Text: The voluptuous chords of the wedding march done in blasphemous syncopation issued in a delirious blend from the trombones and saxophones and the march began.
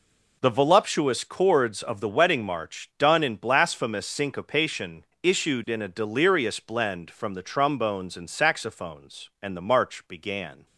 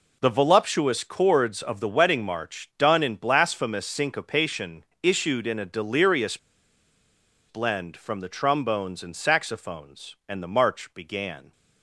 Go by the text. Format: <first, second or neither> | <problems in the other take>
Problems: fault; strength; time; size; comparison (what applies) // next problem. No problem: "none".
first | pauses between "syncopation" and "issued"; slight; at 4.8 s; 0.16 s long; slight in the first // pauses between "delirious" and "blend"; at 6.3 s; 1.1 s long